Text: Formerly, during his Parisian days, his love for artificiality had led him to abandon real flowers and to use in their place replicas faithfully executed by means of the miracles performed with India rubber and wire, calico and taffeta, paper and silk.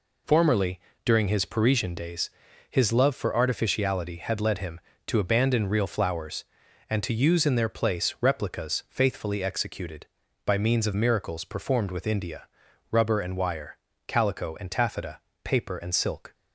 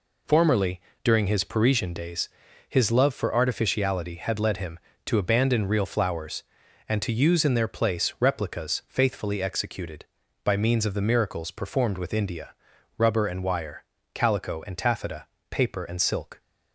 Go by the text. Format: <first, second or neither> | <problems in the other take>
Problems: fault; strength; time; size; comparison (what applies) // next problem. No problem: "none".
second | skips "the"; at 10.9 s // pauses between "India" and "rubber"; at 12.4 s; 0.42 s long; also in the second